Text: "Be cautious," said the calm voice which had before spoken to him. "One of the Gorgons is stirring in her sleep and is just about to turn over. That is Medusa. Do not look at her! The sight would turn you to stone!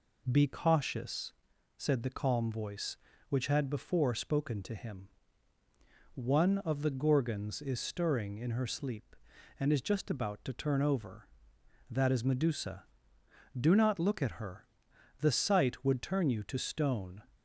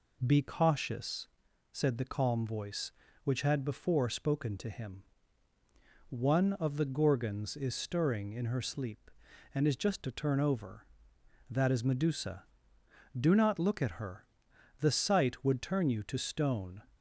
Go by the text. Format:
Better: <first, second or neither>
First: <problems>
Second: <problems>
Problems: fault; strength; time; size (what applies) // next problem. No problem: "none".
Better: first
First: none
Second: skips "about"; at 10.0 s